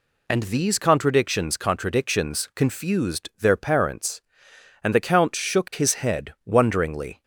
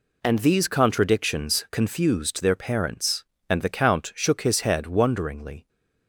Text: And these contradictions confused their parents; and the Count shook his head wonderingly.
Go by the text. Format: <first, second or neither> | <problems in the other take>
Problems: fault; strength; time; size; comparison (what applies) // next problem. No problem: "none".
second | says "contradictions" twice; at 1.5 s